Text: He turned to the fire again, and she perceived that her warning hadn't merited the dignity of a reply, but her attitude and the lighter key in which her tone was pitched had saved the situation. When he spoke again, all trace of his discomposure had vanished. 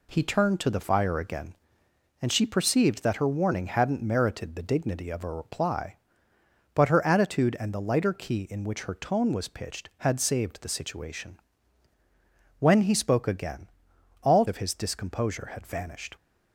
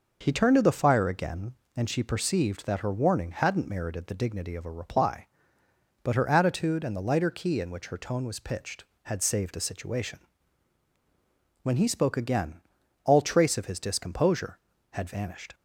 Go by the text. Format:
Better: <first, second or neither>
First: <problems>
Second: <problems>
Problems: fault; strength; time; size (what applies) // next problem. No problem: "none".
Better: second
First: skips "trace"; at 14.4 s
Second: none